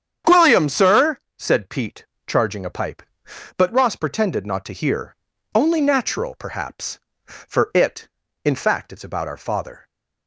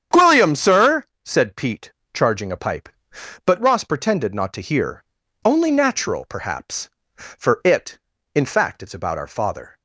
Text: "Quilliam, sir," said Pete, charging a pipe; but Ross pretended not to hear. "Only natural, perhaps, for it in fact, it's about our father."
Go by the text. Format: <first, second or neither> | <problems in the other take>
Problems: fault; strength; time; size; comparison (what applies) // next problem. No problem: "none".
neither | starts louder than the rest; strong; the same in both